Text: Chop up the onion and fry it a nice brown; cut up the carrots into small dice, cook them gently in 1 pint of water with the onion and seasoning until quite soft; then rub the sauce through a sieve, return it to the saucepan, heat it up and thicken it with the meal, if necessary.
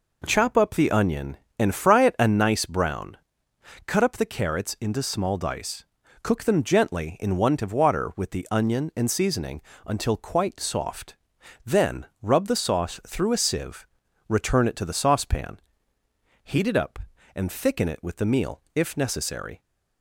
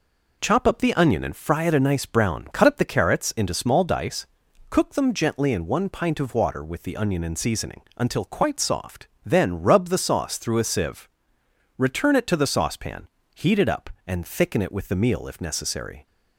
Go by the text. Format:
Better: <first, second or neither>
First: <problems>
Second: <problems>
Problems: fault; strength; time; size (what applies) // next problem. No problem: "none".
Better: second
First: skips "pint"; at 7.5 s // pauses between "seasoning" and "until"; slight; at 9.6 s; 0.24 s long // pauses between "then" and "rub"; slight; at 12.0 s; 0.18 s long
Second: pauses between "seasoning" and "until"; slight; at 7.7 s; 0.16 s long